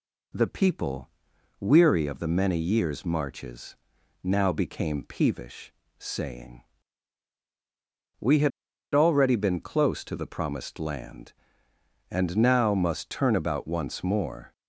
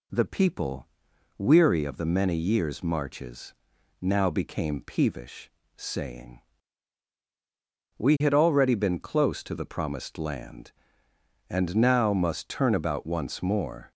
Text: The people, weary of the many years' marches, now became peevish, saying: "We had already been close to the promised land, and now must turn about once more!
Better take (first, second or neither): second